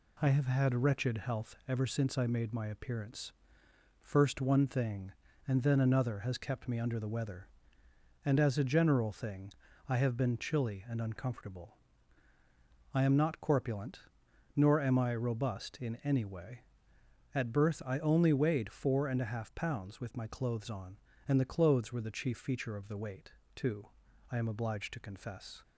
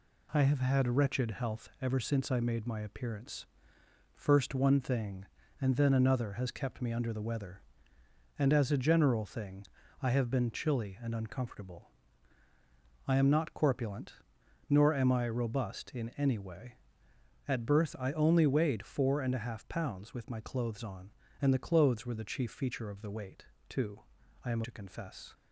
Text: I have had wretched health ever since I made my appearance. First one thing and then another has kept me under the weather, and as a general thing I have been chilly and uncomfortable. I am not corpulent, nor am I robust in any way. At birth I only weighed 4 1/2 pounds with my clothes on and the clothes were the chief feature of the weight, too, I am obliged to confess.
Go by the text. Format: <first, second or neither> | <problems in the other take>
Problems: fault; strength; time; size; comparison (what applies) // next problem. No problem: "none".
first | pauses between "thing" and "I"; slight; at 9.6 s; 0.34 s long; slight in the first // skips "obliged"; at 24.6 s